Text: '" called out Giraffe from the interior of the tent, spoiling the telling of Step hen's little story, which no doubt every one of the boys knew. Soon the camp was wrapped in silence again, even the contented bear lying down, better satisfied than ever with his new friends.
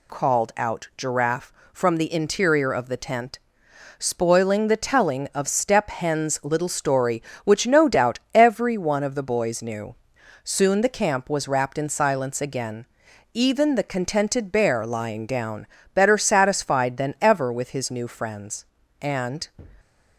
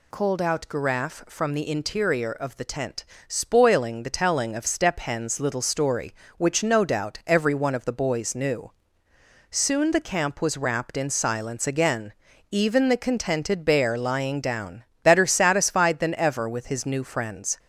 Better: second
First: pauses between "doubt" and "every"; slight; at 8.1 s; 0.16 s long // goes on to say "And"; slight; from 19.0 s on; 0.46 s long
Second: none

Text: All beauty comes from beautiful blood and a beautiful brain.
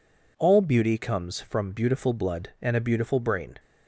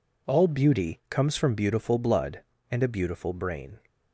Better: neither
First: none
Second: none

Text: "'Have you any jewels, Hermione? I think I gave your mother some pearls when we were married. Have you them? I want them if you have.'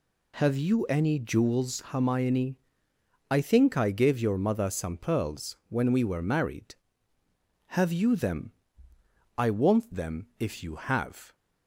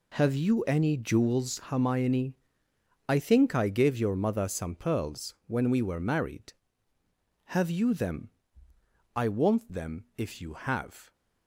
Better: first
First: none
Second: gets quieter; strong; throughout; 12 dB

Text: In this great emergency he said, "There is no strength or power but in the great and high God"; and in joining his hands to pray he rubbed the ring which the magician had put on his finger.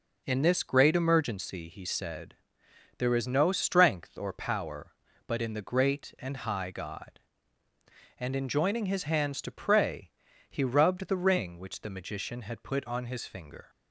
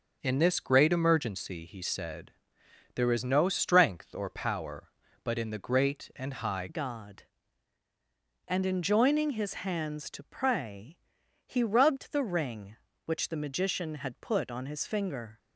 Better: first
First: pauses between "pray" and "he"; slight; at 10.1 s; 0.36 s long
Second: starts louder than the rest; until 1.2 s; 6.5 dB // changes voice at "God"; from 6.6 s on; 8.7 s long // pauses between "pray" and "he"; noticeable; at 10.9 s; 0.48 s long

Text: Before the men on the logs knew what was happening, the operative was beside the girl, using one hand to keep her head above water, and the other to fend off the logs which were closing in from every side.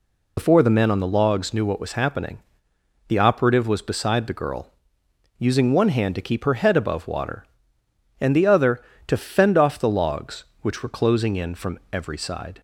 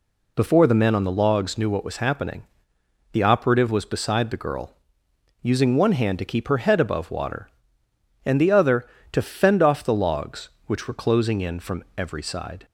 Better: second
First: loses the start of "Before"; at 0.3 s; 55 ms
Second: none

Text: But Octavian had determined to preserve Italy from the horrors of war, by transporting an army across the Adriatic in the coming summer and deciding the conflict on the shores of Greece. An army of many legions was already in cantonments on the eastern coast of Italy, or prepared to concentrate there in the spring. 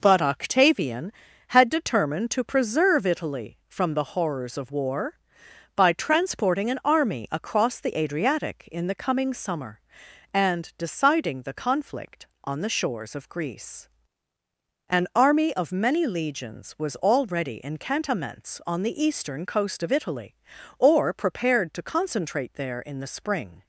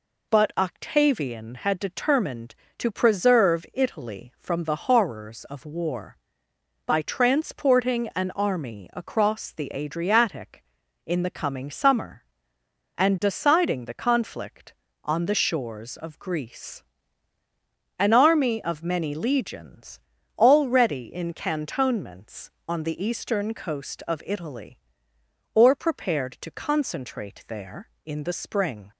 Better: first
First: none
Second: skips "was"; at 20.1 s

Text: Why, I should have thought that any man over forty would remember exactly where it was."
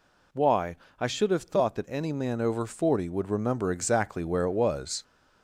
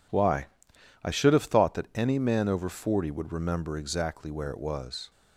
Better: second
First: gets louder; slight; throughout; 2 dB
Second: none

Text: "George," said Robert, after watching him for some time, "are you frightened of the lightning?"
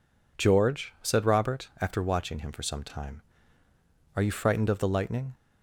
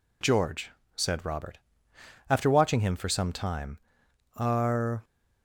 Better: first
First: none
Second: stops before "you frightened of the lightning"; at 5.0 s

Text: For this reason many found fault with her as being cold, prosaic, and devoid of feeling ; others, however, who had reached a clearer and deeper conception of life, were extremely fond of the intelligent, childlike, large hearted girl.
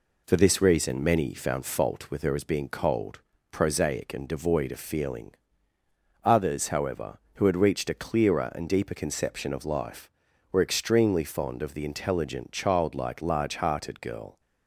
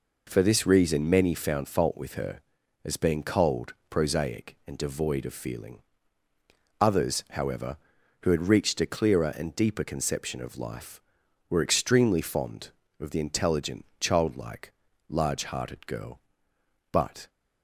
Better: first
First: none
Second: goes on to say "But"; slight; from 16.9 s on; 0.38 s long

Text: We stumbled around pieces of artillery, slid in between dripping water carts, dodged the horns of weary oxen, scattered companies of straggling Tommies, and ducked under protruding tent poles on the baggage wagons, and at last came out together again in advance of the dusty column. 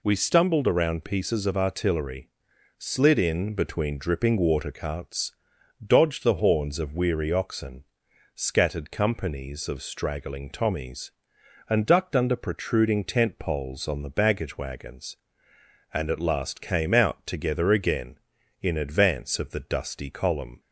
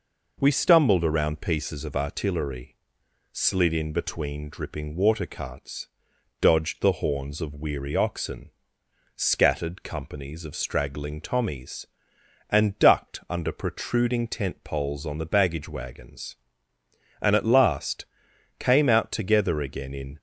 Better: first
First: none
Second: pauses between "last" and "came"; noticeable; at 18.0 s; 0.54 s long // stops before "advance of the dusty column"; at 20.1 s

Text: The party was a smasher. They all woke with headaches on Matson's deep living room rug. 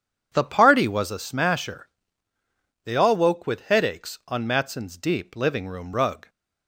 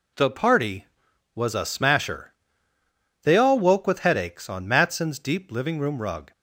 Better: neither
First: none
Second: none

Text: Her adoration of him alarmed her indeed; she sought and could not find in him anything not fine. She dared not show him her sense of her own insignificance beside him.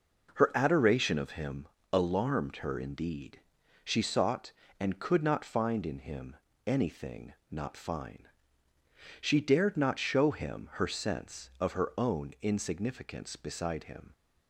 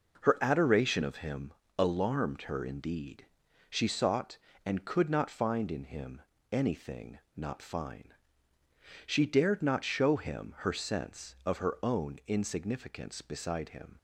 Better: neither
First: pauses between "him" and "alarmed"; slight; at 1.6 s; 0.26 s long // pauses between "him" and "anything"; slight; at 6.3 s; 0.30 s long // pauses between "anything" and "not"; slight; at 7.3 s; 0.18 s long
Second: pauses between "him" and "alarmed"; slight; at 1.5 s; 0.26 s long // pauses between "him" and "anything"; slight; at 6.2 s; 0.30 s long // pauses between "anything" and "not"; slight; at 7.1 s; 0.18 s long

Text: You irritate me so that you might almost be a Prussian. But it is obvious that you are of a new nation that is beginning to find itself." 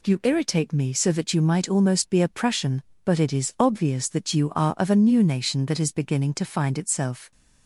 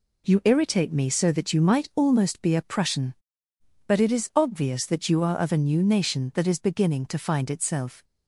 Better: neither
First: none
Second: none

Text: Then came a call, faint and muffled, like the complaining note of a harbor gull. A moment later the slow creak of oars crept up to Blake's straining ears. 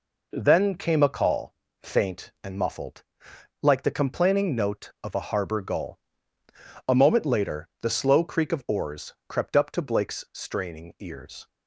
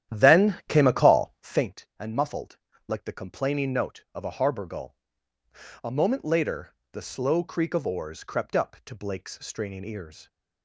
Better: first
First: none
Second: starts louder than the rest; strong; until 1.8 s; 11 dB // pauses between "later" and "the"; slight; at 6.7 s; 0.16 s long

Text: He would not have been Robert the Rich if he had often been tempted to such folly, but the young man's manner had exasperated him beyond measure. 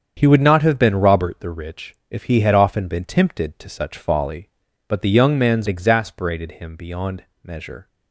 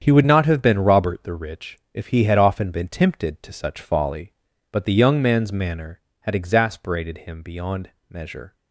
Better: second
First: starts louder than the rest; strong; until 1.1 s; 7.5 dB // pauses between "Rich" and "if"; slight; at 1.9 s; 0.16 s long // skips "manner had"; at 5.6 s // pauses between "beyond" and "measure"; slight; at 7.2 s; 0.18 s long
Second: starts louder than the rest; strong; until 1.0 s; 8 dB // pauses between "Rich" and "if"; slight; at 1.7 s; 0.16 s long // pauses between "beyond" and "measure"; slight; at 7.9 s; 0.18 s long

